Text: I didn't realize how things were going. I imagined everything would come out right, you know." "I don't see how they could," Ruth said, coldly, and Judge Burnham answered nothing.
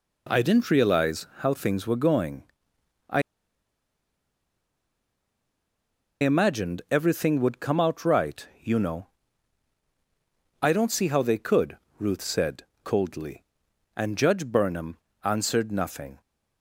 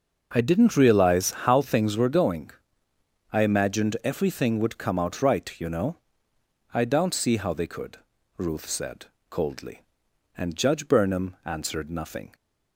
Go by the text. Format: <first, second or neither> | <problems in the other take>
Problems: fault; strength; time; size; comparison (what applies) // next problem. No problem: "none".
second | pauses between "I" and "imagined"; strong; at 3.2 s; 2.9 s long // pauses between "Burnham" and "answered"; slight; at 14.9 s; 0.28 s long